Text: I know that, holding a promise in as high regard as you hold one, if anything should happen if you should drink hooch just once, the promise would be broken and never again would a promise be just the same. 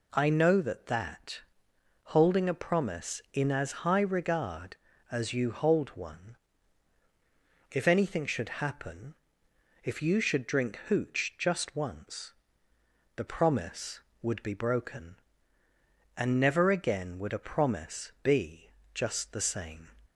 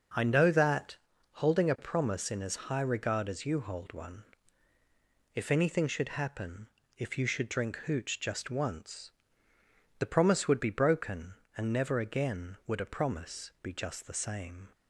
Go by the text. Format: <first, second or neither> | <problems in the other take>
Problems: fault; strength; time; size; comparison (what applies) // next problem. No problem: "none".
second | says "that" twice; at 0.8 s // pauses between "happen" and "if"; noticeable; at 9.1 s; 0.70 s long; slight in the second // pauses between "be" and "just"; slight; at 18.7 s; 0.22 s long